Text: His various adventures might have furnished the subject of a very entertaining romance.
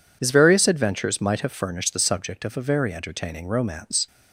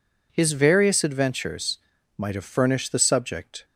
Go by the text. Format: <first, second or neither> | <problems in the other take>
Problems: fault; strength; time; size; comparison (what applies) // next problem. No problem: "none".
first | pauses between "adventures" and "might"; at 1.7 s; 0.38 s long // stops before "of a very entertaining romance"; at 3.6 s